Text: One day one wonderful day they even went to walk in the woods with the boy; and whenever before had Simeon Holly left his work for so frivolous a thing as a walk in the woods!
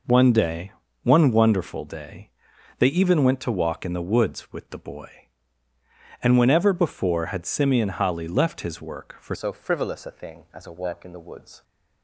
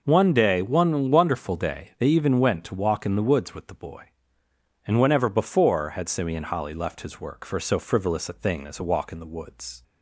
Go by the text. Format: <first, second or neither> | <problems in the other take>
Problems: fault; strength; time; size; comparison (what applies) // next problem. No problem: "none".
second | pauses between "day" and "one"; slight; at 0.7 s; 0.30 s long // pauses between "day" and "they"; noticeable; at 2.2 s; 0.50 s long // changes voice at "so"; from 9.3 s on; 2.3 s long